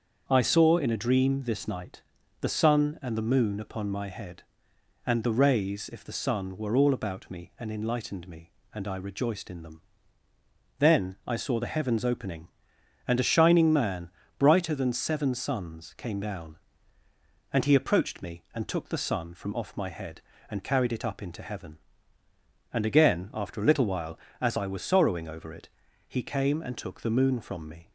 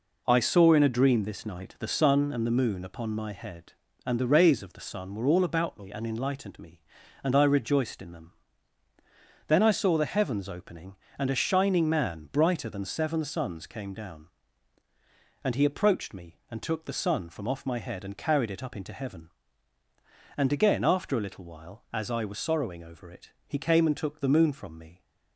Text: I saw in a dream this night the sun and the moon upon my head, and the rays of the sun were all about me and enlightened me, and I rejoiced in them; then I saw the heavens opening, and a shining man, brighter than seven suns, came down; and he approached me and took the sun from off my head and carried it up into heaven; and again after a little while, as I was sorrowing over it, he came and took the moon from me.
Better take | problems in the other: second | starts louder than the rest; until 1.2 s; 6.5 dB // pauses between "night" and "the"; at 2.0 s; 0.38 s long // says "if" for "of"; at 5.9 s

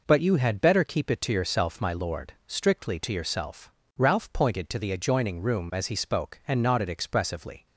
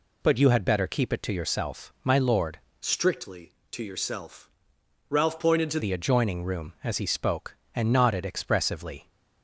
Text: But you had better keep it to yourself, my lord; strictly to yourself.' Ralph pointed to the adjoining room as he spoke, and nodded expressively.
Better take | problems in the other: first | changes voice from "strictly" to "to"; from 2.8 to 5.7 s; 2.9 s long

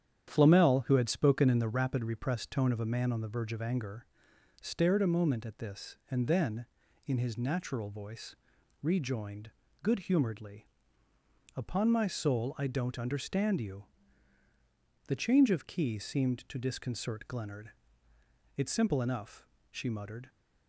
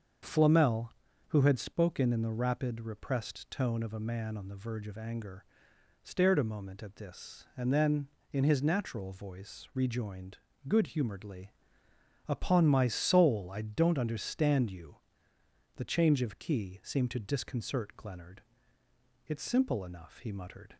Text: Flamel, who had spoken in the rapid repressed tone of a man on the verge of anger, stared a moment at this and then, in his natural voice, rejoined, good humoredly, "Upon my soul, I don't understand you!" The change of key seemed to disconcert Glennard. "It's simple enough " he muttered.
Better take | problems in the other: second | starts louder than the rest; strong; until 1.3 s; 9 dB; also in the second // says "she" for "he"; at 19.7 s

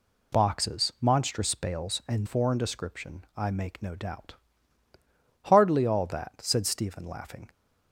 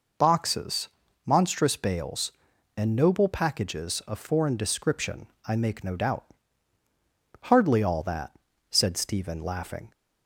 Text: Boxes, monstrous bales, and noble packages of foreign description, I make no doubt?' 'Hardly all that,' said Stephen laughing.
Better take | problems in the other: second | skips "noble packages of"; at 2.2 s

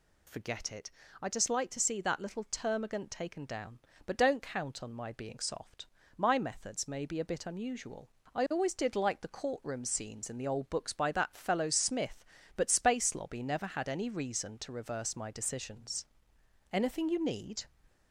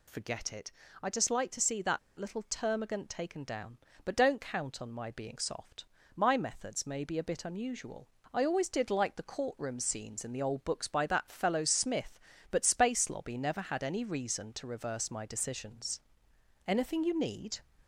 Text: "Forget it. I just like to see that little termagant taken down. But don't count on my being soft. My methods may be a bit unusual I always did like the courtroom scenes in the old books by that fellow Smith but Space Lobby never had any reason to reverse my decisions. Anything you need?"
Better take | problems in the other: first | pauses between "that" and "little"; slight; at 1.9 s; 0.19 s long // pauses between "unusual" and "I"; slight; at 8.0 s; 0.26 s long; slight in the first

